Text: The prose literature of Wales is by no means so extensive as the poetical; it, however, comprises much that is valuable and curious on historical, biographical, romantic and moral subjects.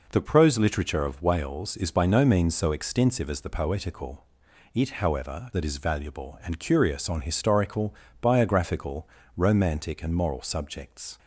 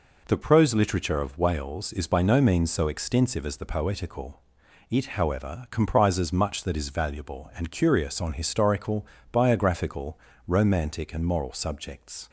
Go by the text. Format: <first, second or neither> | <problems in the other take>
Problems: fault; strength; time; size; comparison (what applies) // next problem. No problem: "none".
second | skips "comprises much"; at 5.5 s